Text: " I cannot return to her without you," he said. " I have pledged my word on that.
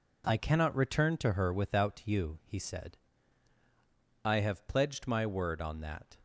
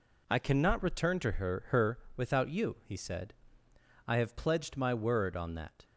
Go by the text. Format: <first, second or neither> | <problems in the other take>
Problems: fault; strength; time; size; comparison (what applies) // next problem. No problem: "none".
first | says "her" twice; at 1.6 s